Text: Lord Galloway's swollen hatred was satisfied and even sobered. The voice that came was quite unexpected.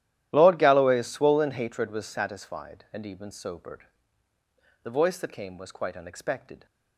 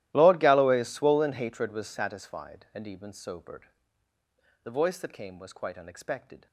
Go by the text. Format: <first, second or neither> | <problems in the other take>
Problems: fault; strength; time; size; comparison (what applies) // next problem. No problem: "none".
first | gets quieter; strong; throughout; 22 dB // starts louder than the rest; strong; until 1.1 s; 14.5 dB; strong in the first